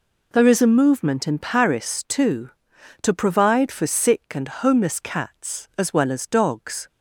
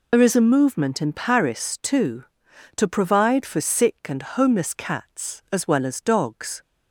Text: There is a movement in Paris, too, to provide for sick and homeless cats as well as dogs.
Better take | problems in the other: first | loses the start of "There"; at 0.1 s; 70 ms

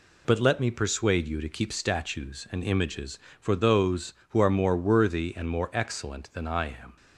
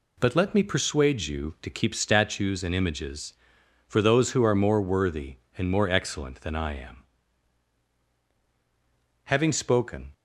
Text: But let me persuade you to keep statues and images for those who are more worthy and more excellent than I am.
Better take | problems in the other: first | goes on to say "Having spoken"; noticeable; from 9.2 s on; 0.88 s long

